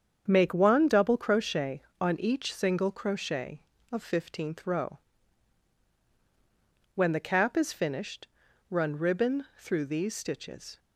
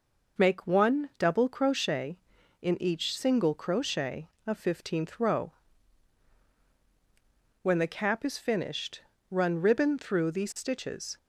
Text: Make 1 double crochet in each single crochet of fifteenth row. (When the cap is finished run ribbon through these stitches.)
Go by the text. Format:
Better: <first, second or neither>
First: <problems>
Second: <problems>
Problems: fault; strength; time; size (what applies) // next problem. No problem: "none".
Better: second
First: starts louder than the rest; strong; until 1.3 s; 7.5 dB // says "on" for "in"; at 2.0 s // pauses between "finished" and "run"; at 8.2 s; 0.44 s long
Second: pauses between "finished" and "run"; slight; at 9.0 s; 0.30 s long